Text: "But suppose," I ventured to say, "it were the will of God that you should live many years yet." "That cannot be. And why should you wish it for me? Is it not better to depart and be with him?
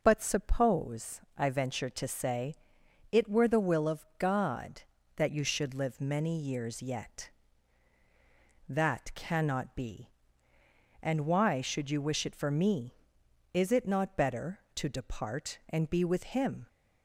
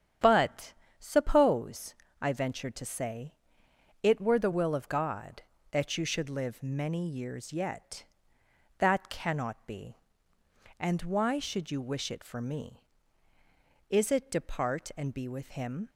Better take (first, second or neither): first